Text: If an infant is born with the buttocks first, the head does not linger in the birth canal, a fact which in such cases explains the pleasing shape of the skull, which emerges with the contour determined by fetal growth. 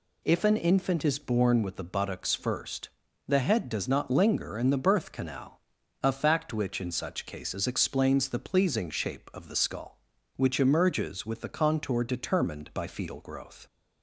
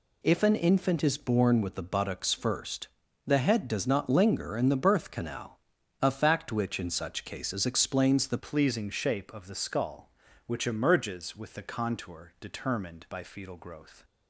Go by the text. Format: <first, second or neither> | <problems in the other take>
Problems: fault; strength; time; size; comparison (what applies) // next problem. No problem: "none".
first | changes voice at "pleasing"; from 8.3 s on; 5.7 s long